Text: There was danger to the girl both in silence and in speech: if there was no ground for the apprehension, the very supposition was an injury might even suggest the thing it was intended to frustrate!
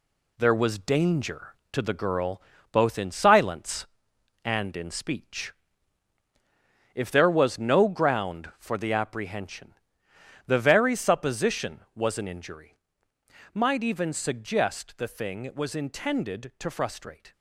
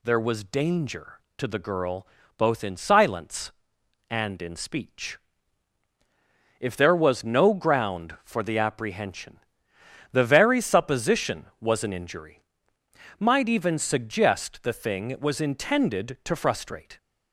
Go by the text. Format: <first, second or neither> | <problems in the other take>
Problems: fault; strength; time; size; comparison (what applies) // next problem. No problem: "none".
second | gets quieter; noticeable; throughout; 6 dB // pauses between "girl" and "both"; slight; at 2.4 s; 0.30 s long; slight in the second // pauses between "injury" and "might"; noticeable; at 12.7 s; 0.78 s long; noticeable in the second